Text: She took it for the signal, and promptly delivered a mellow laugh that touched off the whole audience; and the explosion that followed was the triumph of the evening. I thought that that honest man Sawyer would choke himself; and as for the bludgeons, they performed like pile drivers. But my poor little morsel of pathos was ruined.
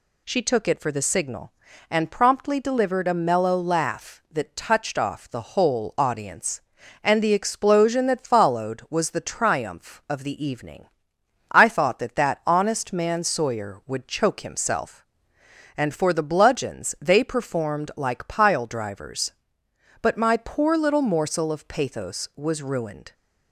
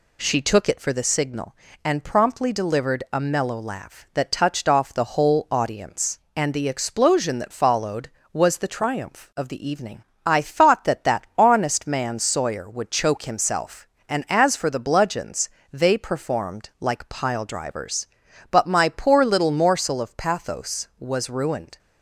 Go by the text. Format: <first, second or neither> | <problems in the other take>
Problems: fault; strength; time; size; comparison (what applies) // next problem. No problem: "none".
second | skips "as"; at 15.9 s